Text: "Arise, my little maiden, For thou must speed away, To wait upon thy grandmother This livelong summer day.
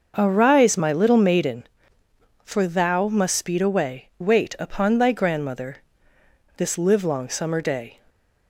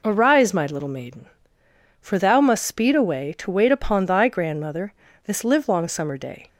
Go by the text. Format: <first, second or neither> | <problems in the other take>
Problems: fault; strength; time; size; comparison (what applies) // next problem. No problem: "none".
second | starts louder than the rest; noticeable; until 1.1 s; 6 dB // skips "To"; at 4.1 s // pauses between "grandmother" and "This"; noticeable; at 5.7 s; 0.78 s long; slight in the second